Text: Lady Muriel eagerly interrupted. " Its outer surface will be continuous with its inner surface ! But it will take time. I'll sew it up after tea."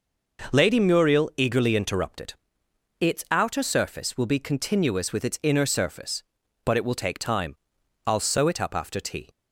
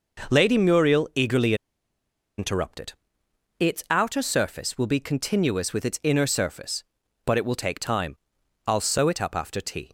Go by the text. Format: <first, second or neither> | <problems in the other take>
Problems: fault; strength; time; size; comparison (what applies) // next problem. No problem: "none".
first | pauses between "eagerly" and "interrupted"; noticeable; at 1.5 s; 0.83 s long